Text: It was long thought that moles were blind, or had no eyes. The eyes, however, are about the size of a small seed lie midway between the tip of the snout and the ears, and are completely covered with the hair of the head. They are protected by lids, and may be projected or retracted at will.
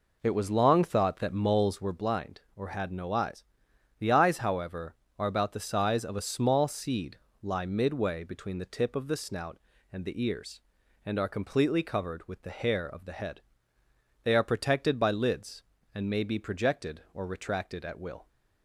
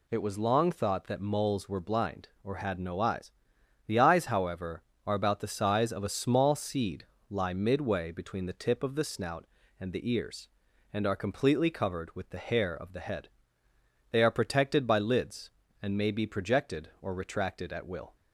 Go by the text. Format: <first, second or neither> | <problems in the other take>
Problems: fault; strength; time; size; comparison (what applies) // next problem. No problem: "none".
second | starts louder than the rest; noticeable; until 2.0 s; 4.5 dB // pauses between "seed" and "lie"; slight; at 7.1 s; 0.24 s long; slight in the second